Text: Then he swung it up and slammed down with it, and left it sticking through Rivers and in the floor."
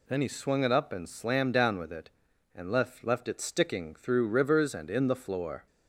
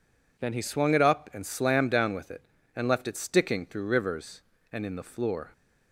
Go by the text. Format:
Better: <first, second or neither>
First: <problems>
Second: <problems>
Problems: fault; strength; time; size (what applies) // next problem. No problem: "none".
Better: second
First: says "left" twice; at 3.0 s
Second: none